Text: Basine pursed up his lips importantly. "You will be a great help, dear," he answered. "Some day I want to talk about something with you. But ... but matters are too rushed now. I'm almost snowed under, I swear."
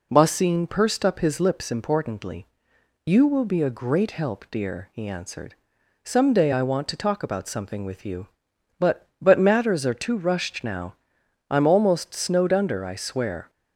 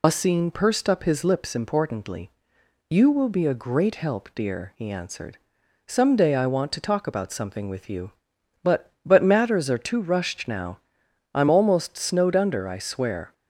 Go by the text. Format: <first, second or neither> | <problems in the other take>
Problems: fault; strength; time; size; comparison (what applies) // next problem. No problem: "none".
first | loses the start of "Basine"; at 0.0 s; 90 ms